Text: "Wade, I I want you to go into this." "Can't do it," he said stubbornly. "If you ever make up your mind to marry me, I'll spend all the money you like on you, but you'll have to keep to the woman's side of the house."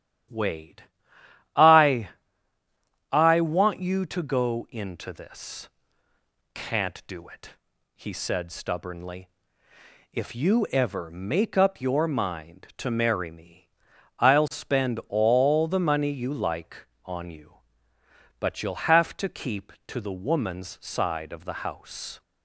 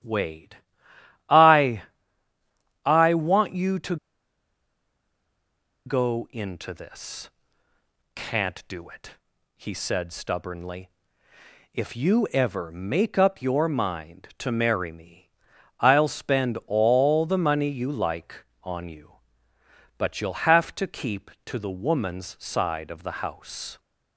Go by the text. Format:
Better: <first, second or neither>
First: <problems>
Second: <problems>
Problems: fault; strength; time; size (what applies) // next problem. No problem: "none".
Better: first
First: starts louder than the rest; strong; until 2.0 s; 11 dB // pauses between "I" and "I"; at 2.0 s; 1.0 s long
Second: starts louder than the rest; strong; until 1.7 s; 11 dB // pauses between "I" and "I"; at 1.8 s; 1.0 s long // pauses between "to" and "go"; strong; at 3.9 s; 1.9 s long